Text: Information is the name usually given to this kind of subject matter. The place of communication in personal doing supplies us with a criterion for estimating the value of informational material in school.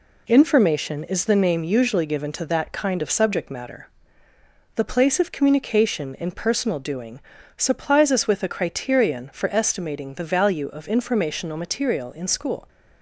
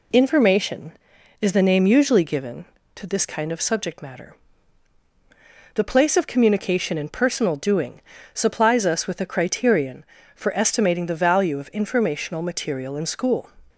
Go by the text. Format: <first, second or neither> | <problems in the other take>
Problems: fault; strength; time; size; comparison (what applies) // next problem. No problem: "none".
second | says "that" for "this"; at 2.4 s // pauses between "doing" and "supplies"; at 7.1 s; 0.38 s long; slight in the second